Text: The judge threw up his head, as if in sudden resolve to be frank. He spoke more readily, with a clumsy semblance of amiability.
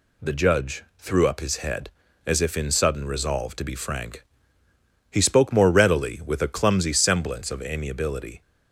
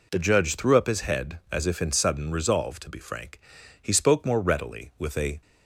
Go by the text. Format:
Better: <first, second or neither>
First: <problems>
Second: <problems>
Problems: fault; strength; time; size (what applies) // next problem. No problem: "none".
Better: first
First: none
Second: stops before "clumsy semblance of amiability"; at 5.4 s